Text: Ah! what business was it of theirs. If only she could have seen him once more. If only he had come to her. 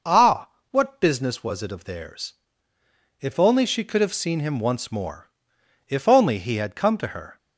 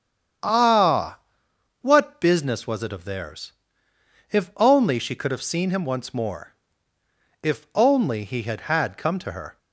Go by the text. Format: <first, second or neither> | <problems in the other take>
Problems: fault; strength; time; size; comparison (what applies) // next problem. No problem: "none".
first | starts louder than the rest; strong; until 2.0 s; 8.5 dB // says "had" twice; at 8.6 s